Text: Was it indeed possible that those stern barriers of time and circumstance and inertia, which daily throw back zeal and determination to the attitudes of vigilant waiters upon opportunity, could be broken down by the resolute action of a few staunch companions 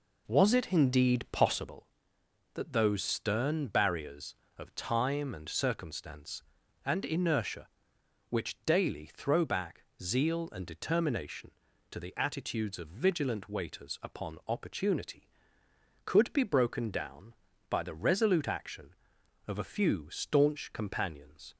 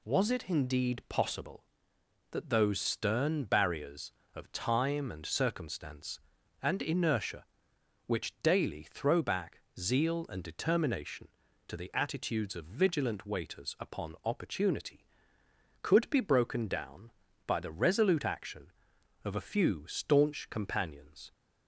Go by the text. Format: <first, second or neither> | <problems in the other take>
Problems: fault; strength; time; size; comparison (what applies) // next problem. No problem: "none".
second | starts louder than the rest; noticeable; until 1.8 s; 4 dB // pauses between "back" and "zeal"; slight; at 9.8 s; 0.18 s long; slight in the second